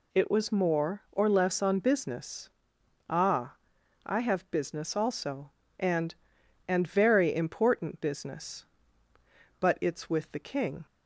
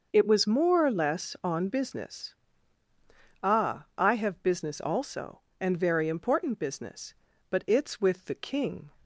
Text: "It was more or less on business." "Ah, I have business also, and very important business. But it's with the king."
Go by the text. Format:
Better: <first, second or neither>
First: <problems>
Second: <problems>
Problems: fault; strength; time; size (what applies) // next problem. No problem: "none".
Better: second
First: says "and" twice; at 6.6 s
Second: none